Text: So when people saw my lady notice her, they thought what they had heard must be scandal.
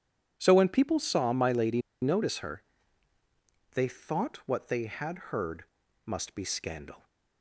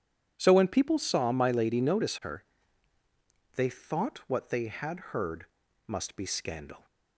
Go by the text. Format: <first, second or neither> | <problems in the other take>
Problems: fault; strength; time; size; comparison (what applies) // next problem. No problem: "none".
second | pauses between "lady" and "notice"; slight; at 1.8 s; 0.21 s long // pauses between "heard" and "must"; at 5.6 s; 0.40 s long; also in the second